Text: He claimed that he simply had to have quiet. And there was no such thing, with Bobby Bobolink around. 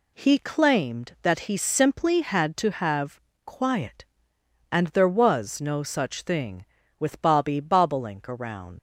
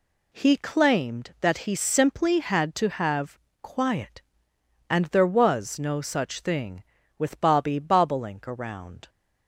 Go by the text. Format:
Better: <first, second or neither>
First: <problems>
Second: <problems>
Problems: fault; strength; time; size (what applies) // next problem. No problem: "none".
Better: second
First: pauses between "have" and "quiet"; slight; at 3.2 s; 0.24 s long // leaves "around" unfinished; at 8.7 s; 110 ms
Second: pauses between "have" and "quiet"; slight; at 3.3 s; 0.22 s long